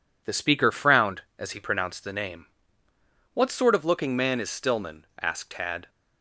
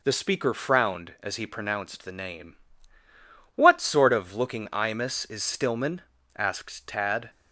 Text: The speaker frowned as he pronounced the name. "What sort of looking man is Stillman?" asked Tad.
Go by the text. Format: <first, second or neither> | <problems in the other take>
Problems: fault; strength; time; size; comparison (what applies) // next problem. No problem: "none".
first | says "imus" for "man"; at 4.7 s